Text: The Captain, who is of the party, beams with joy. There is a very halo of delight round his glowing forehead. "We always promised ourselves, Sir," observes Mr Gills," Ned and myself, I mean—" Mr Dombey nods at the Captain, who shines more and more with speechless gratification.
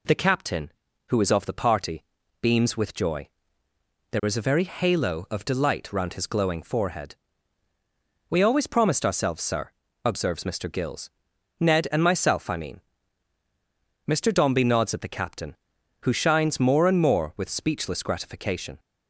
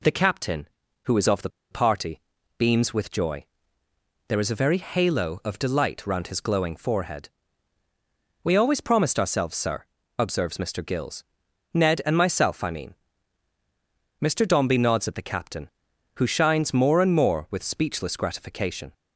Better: first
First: none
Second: pauses between "the" and "party"; slight; at 1.4 s; 0.22 s long

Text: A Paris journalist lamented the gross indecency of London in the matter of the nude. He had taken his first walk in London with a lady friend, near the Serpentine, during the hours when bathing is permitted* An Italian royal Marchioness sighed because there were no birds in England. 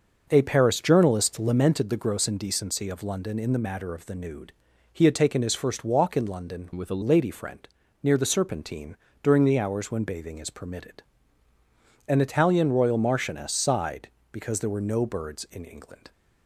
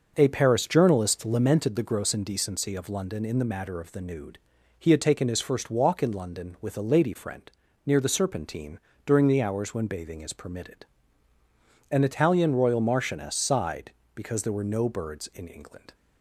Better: second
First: starts louder than the rest; noticeable; until 1.3 s; 6 dB // changes voice from "with" to "a"; from 6.7 to 7.0 s; 0.3 s long // pauses between "permitted" and "An"; at 11.0 s; 1.0 s long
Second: pauses between "permitted" and "An"; at 10.8 s; 1.0 s long

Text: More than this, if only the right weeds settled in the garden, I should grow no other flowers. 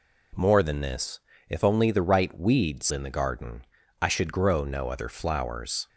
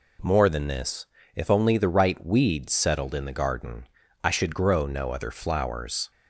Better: second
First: skips "settled"; at 2.8 s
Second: none

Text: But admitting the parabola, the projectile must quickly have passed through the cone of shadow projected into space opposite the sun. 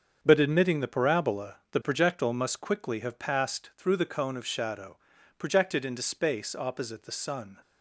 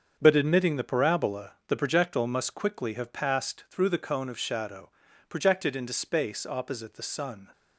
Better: neither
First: starts louder than the rest; strong; until 1.2 s; 7 dB // pauses between "shadow" and "projected"; at 4.9 s; 0.40 s long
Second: starts louder than the rest; until 1.2 s; 7 dB // pauses between "shadow" and "projected"; at 4.8 s; 0.38 s long

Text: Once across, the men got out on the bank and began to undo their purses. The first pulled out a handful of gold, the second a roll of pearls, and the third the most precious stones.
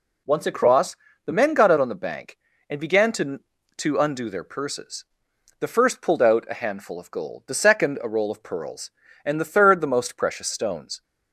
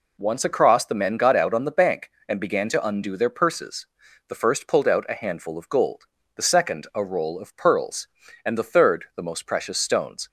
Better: second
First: says "to" twice; at 3.7 s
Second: none

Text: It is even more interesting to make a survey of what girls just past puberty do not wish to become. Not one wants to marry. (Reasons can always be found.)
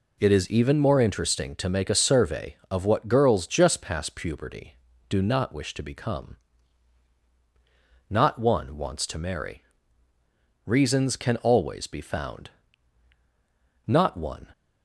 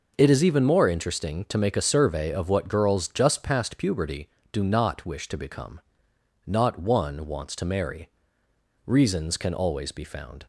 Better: second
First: goes on to say "Not one"; noticeable; from 13.8 s on; 0.62 s long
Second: none

